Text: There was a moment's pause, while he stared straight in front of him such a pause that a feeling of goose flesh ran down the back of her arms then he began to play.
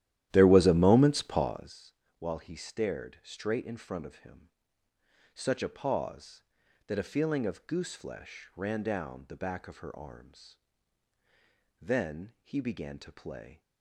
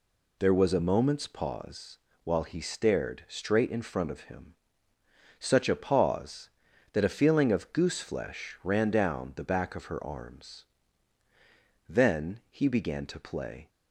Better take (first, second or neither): second